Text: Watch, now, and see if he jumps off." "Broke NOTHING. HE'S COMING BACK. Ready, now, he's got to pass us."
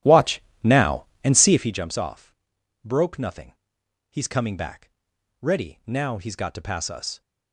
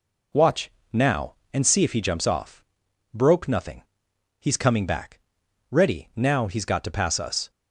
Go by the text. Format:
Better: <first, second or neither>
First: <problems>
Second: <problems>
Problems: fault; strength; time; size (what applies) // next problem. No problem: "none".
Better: second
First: starts louder than the rest; strong; until 1.8 s; 12.5 dB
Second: none